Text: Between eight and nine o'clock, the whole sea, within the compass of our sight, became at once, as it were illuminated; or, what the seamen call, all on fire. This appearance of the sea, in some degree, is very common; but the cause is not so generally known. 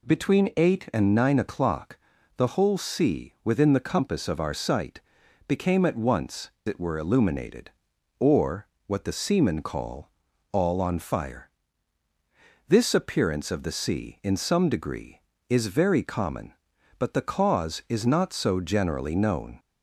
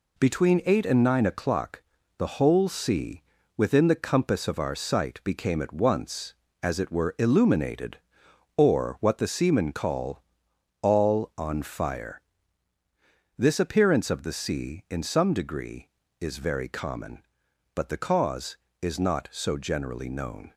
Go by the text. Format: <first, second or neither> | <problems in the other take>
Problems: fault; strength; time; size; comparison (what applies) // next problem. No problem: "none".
second | skips "as"; at 6.5 s